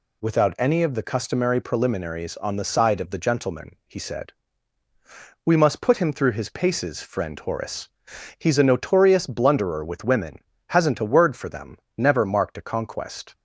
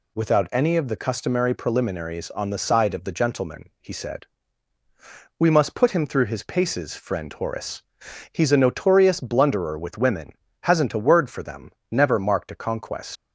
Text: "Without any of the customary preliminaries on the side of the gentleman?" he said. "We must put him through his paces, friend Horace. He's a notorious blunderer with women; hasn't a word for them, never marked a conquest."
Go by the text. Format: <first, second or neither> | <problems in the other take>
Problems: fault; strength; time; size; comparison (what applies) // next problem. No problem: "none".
first | leaves "conquest" unfinished; at 13.1 s; 120 ms